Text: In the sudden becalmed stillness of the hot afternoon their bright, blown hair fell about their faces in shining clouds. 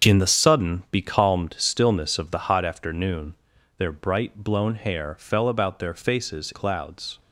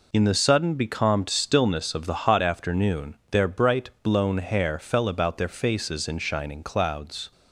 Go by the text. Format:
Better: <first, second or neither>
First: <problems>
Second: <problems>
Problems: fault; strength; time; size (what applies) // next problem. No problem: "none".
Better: second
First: starts louder than the rest; until 1.1 s; 7 dB // pauses between "afternoon" and "their"; at 3.3 s; 0.42 s long // skips "in shining"; at 6.5 s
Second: none